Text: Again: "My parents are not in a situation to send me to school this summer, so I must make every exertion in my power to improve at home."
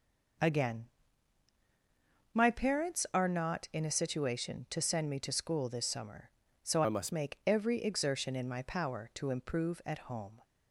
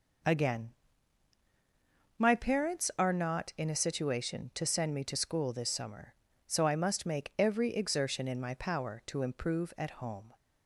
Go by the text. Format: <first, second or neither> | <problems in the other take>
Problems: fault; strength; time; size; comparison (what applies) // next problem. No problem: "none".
second | changes voice from "I" to "must"; from 6.8 to 7.1 s; 0.3 s long